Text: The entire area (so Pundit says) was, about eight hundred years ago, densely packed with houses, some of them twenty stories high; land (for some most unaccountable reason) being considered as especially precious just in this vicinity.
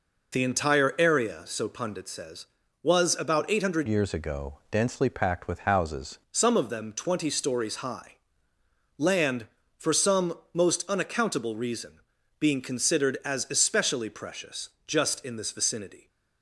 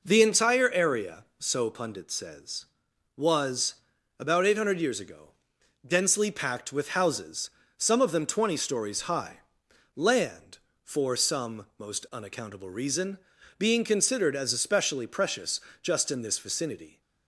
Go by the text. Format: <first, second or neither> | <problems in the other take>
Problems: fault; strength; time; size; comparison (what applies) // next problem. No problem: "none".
second | changes voice from "years" to "houses"; from 3.8 to 6.1 s; 2.3 s long // pauses between "some" and "most"; slight; at 10.3 s; 0.16 s long // pauses between "precious" and "just"; slight; at 14.6 s; 0.16 s long; slight in the second